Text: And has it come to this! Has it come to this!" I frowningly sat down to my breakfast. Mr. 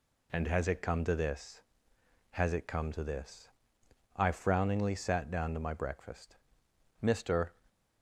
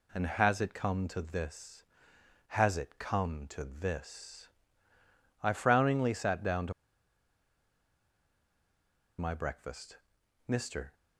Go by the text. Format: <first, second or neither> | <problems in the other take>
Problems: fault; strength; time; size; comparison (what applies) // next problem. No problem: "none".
first | pauses between "to" and "my"; strong; at 6.7 s; 2.4 s long